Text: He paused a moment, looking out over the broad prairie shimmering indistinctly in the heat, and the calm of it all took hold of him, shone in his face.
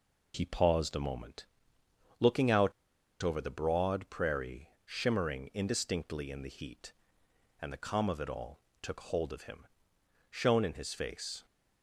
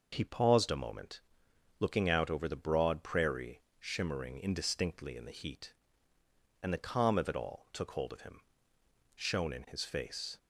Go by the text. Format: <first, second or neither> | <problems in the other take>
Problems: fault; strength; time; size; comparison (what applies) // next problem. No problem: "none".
second | pauses between "out" and "over"; noticeable; at 2.7 s; 0.50 s long // pauses between "prairie" and "shimmering"; slight; at 4.6 s; 0.16 s long; slight in the second // pauses between "all" and "took"; slight; at 8.5 s; 0.22 s long